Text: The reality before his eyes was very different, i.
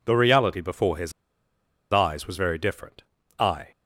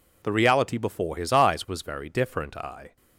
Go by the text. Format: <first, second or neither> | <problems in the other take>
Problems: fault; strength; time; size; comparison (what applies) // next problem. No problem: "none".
second | pauses between "his" and "eyes"; noticeable; at 1.1 s; 0.80 s long